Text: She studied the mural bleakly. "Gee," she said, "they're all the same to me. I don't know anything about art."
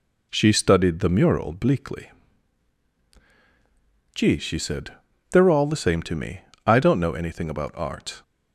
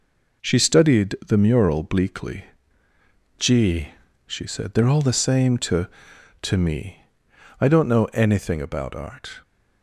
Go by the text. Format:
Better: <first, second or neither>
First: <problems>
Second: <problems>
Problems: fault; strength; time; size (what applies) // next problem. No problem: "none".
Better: first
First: none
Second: says "to" twice; at 6.4 s